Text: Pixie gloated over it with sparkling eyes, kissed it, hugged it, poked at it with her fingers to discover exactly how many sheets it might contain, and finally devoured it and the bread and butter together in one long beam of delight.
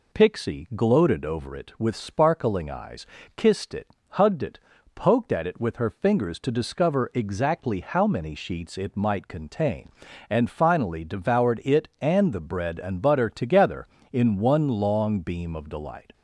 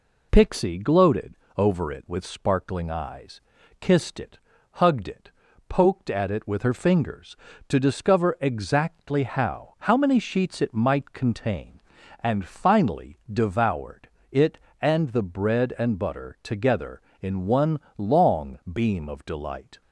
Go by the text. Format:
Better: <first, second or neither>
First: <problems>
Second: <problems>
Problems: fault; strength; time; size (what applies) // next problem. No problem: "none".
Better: first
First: none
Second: pauses between "gloated" and "over"; slight; at 1.3 s; 0.22 s long // says "how" twice; at 9.8 s // pauses between "finally" and "devoured"; slight; at 13.1 s; 0.16 s long // pauses between "devoured" and "it"; slight; at 14.0 s; 0.22 s long // pauses between "one" and "long"; slight; at 17.8 s; 0.18 s long